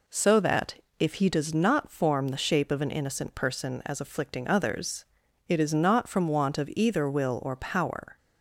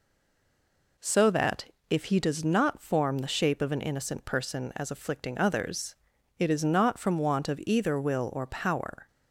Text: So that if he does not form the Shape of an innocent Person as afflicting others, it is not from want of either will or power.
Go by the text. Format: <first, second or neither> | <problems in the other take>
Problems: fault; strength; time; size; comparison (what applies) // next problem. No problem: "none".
first | stays silent before the first word; until 0.9 s; 0.9 s long // pauses between "that" and "if"; slight; at 1.6 s; 0.24 s long; slight in the first